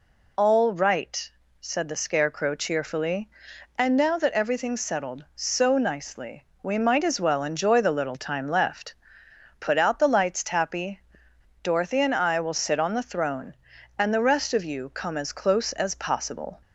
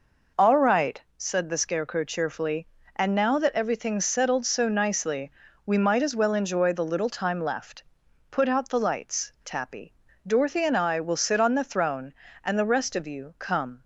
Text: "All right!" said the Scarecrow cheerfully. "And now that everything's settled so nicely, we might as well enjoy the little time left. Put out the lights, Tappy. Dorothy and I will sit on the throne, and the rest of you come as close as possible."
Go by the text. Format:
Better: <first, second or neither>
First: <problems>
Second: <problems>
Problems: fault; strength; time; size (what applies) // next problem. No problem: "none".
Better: first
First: none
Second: stops before "as close as possible"; at 13.8 s